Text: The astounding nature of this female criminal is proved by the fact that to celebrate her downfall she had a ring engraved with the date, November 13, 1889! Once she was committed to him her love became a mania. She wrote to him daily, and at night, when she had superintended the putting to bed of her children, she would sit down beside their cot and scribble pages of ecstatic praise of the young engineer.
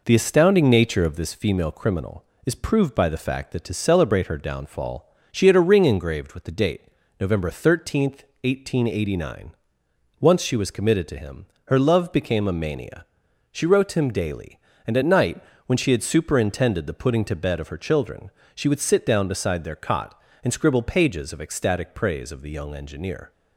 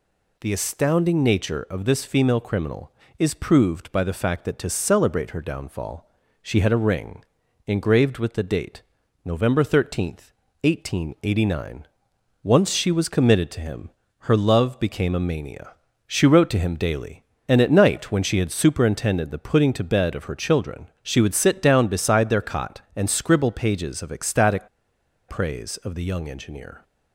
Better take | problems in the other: first | pauses between "downfall" and "she"; slight; at 6.0 s; 0.32 s long; slight in the first // pauses between "ring" and "engraved"; at 7.2 s; 0.42 s long // pauses between "him" and "her"; slight; at 13.8 s; 0.30 s long; slight in the first // pauses between "ecstatic" and "praise"; noticeable; at 24.6 s; 0.60 s long

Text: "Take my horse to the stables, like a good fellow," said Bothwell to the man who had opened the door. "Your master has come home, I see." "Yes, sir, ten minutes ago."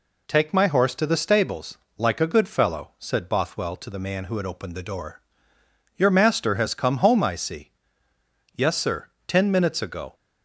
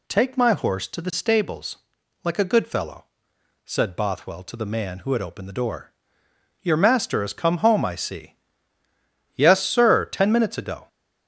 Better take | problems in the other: neither | none

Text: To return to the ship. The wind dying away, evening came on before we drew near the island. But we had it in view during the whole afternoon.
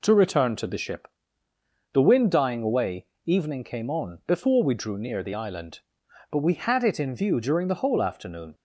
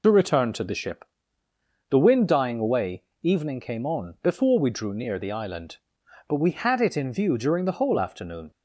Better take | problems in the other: first | loses the start of "To"; at 0.0 s; 45 ms

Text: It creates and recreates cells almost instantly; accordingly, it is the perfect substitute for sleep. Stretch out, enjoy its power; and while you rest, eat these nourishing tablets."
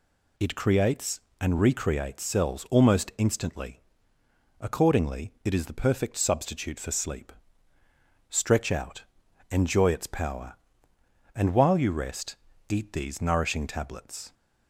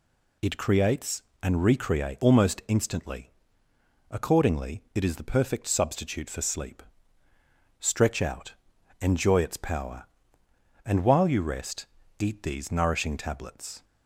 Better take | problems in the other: first | skips "cells"; at 2.2 s

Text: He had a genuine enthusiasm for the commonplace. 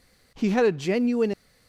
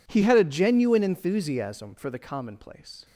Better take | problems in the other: second | stops before "enthusiasm for the commonplace"; at 1.3 s

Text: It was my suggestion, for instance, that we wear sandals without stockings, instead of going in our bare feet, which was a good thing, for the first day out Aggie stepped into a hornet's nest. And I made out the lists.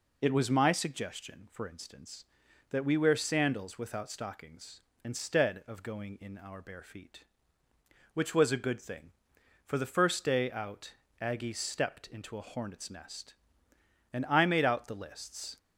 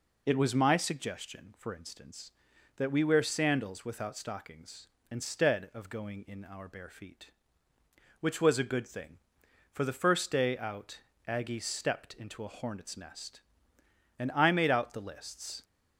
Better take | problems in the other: neither | pauses between "out" and "Aggie"; slight; the same in both

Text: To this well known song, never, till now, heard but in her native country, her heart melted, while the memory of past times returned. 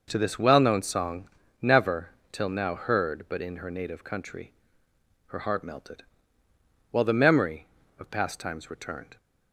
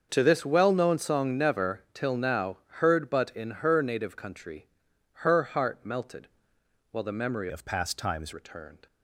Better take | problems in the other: first | starts louder than the rest; until 1.1 s; 6.5 dB // changes voice from "of" to "times"; from 7.4 to 8.3 s; 0.9 s long

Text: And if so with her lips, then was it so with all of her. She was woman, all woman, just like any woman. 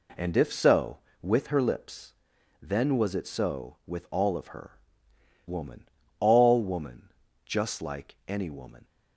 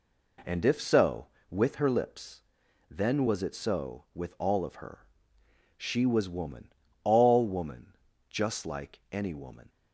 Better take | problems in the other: second | skips "She was"; at 5.1 s

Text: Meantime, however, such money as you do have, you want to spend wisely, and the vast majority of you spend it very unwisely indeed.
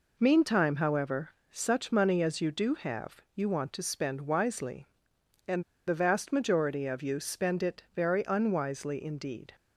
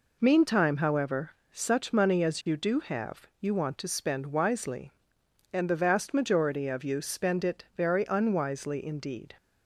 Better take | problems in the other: second | pauses between "and" and "the"; slight; at 5.6 s; 0.24 s long

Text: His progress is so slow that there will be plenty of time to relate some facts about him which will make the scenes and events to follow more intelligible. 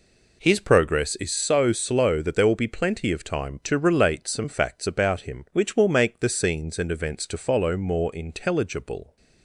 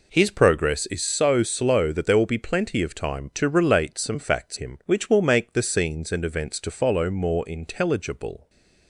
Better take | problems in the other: first | skips "about"; at 4.5 s

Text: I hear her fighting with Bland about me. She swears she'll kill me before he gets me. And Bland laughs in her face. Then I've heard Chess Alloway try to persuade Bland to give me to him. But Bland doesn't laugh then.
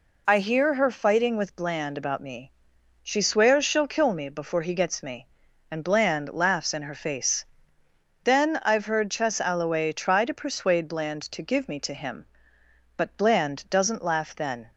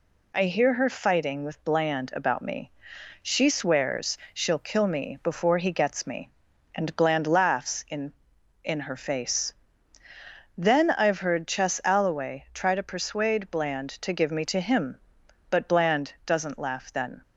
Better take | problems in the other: first | pauses between "swears" and "she'll"; slight; at 4.1 s; 0.16 s long // says "in" twice; at 8.6 s

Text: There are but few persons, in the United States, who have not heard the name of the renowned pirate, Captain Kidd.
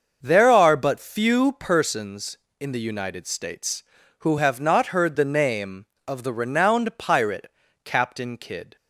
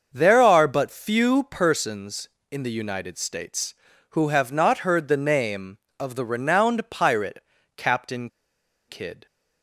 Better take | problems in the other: first | starts louder than the rest; until 1.1 s; 6.5 dB; also in the first // pauses between "Captain" and "Kidd"; noticeable; at 8.2 s; 0.60 s long

